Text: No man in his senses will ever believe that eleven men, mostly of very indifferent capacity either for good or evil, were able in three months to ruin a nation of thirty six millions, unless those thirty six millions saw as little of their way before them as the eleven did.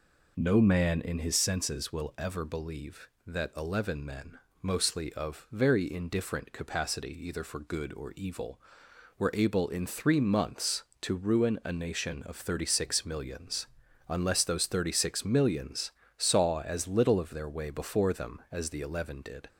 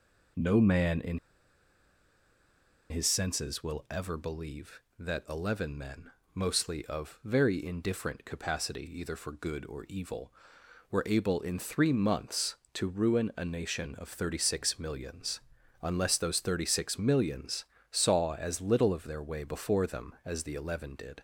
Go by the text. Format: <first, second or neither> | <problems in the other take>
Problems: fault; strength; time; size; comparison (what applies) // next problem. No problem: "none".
first | pauses between "in" and "his"; strong; at 1.1 s; 1.7 s long // pauses between "millions" and "saw"; slight; at 17.6 s; 0.26 s long; slight in the first